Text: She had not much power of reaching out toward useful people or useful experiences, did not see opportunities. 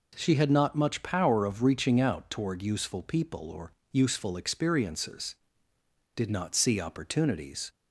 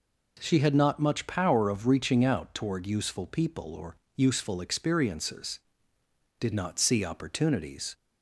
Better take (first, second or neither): neither